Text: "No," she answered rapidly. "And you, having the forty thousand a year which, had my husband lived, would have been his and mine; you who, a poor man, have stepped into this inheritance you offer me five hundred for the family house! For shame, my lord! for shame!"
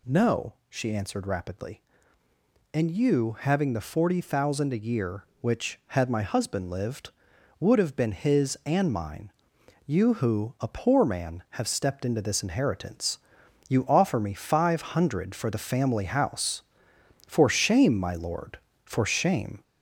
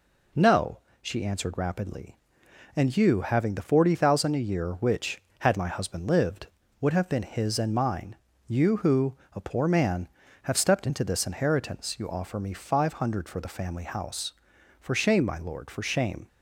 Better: second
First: gets louder; throughout; 3.5 dB // pauses between "inheritance" and "you"; noticeable; at 13.1 s; 0.50 s long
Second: none

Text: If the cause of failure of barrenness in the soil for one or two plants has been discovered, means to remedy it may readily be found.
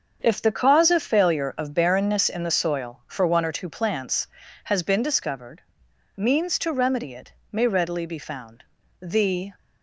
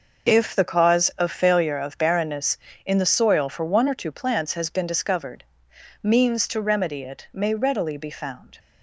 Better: second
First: starts louder than the rest; until 1.2 s; 7 dB // pauses between "it" and "may"; slight; at 7.3 s; 0.22 s long // goes on to say "The"; from 8.9 s on; 0.54 s long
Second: none

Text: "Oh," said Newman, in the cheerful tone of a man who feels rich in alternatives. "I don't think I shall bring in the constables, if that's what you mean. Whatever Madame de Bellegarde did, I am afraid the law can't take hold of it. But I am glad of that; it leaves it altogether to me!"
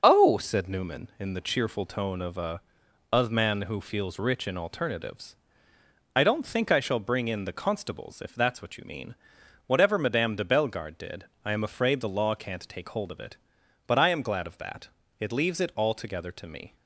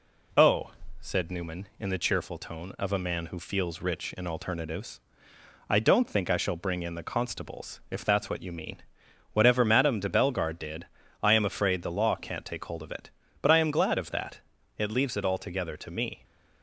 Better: second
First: starts louder than the rest; until 1.0 s; 6.5 dB // says "a" twice; at 3.1 s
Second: none

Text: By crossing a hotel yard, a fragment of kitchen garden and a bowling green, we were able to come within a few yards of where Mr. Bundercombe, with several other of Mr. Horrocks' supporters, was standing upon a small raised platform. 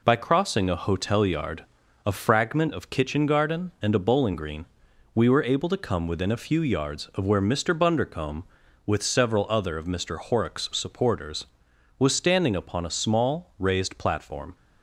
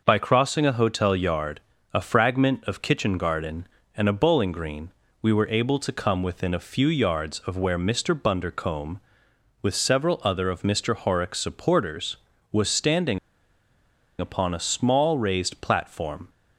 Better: first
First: none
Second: pauses between "standing" and "upon"; at 13.1 s; 1.0 s long

